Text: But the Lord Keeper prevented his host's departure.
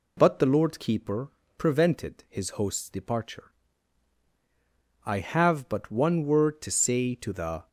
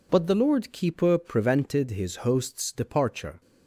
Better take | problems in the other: second | pauses between "Keeper" and "prevented"; slight; at 1.3 s; 0.28 s long // goes on to say "I have but one word to say to the"; strong; from 5.0 s on; 2.6 s long

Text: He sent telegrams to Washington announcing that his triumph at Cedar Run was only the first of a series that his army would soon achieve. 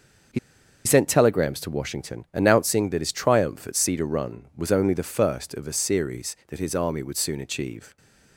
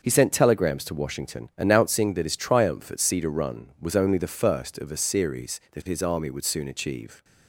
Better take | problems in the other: second | starts louder than the rest; until 1.8 s; 6.5 dB; also in the second // pauses between "He" and "sent"; noticeable; at 0.3 s; 0.47 s long

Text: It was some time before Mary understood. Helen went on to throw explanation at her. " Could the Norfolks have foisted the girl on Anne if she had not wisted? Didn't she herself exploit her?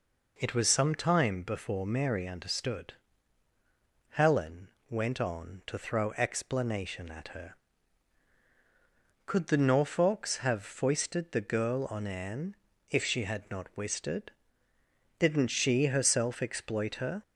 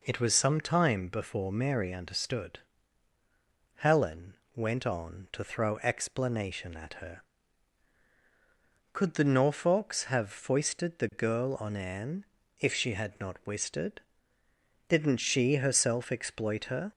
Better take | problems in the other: neither | pauses between "Helen" and "went"; slight; the same in both // pauses between "Anne" and "if"; slight; the same in both

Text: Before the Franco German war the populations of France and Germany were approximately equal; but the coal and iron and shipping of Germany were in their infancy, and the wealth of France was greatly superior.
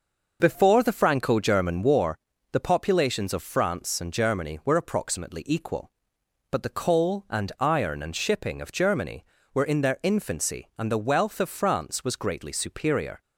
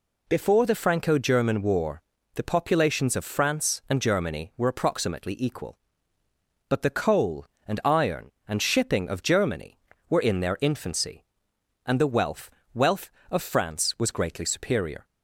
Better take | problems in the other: first | pauses between "war" and "the"; slight; at 2.0 s; 0.34 s long; slight in the first // says "wealth" twice; at 12.7 s

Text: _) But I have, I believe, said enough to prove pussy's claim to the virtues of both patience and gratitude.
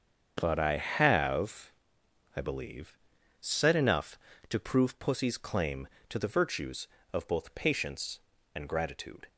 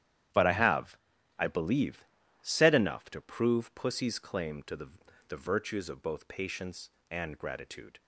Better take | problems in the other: first | starts louder than the rest; strong; until 1.7 s; 10.5 dB; strong in the first // says "the" twice; at 5.2 s

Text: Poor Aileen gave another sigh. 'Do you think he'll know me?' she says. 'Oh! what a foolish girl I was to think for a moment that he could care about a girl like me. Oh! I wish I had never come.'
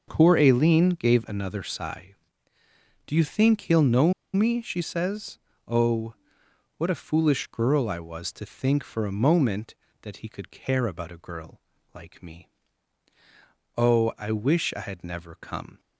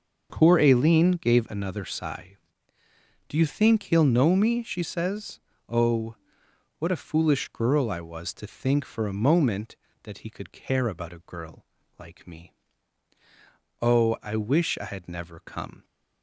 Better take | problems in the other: second | pauses between "know" and "me"; slight; at 4.1 s; 0.20 s long // pauses between "girl" and "like"; slight; at 11.5 s; 0.36 s long; slight in the second

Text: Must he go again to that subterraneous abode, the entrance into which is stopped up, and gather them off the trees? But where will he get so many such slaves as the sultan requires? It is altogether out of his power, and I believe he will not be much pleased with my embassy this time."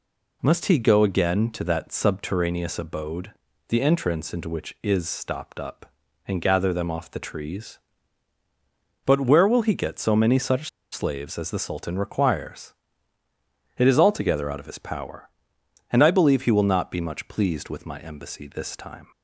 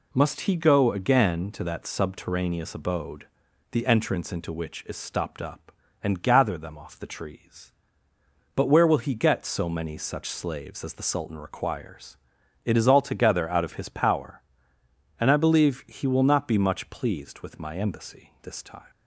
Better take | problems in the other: second | pauses between "such" and "slaves"; slight; at 10.6 s; 0.22 s long

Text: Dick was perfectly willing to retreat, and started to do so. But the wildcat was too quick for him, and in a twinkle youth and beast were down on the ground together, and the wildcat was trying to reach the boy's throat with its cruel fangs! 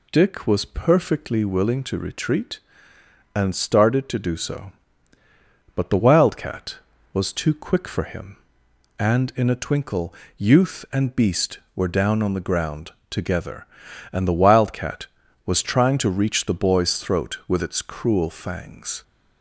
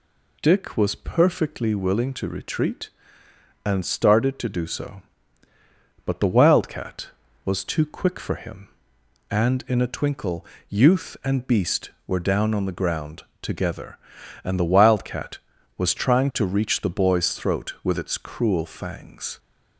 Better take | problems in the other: neither | pauses between "twinkle" and "youth"; slight; the same in both // pauses between "ground" and "together"; slight; the same in both

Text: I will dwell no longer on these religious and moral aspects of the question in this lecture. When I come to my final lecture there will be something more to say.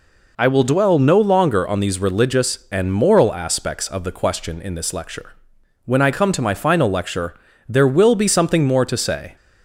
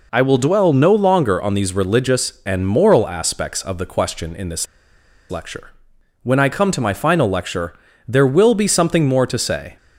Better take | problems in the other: first | pauses between "this" and "lecture"; noticeable; at 4.6 s; 0.64 s long // pauses between "lecture" and "there"; slight; at 7.7 s; 0.34 s long; slight in the first

